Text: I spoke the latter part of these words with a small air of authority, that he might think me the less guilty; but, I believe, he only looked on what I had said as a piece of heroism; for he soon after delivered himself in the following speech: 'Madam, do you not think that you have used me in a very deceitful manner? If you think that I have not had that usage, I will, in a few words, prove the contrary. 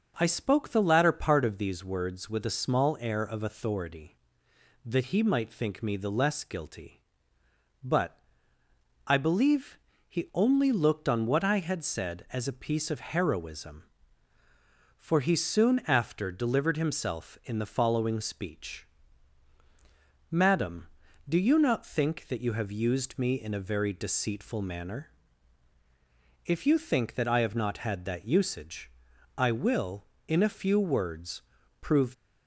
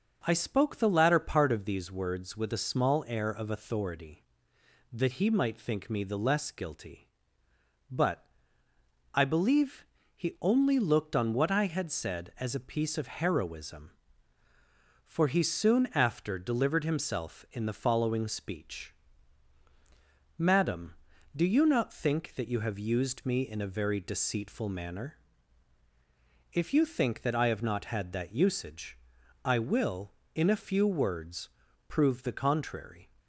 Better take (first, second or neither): second